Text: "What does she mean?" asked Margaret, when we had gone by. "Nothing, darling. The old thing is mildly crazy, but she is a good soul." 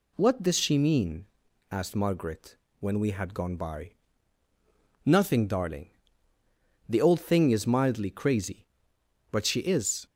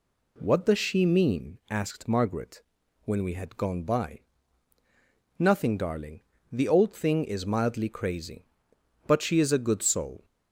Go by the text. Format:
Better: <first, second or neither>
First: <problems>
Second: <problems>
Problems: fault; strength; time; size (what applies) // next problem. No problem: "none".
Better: second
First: stops before "a good soul"; at 10.0 s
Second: none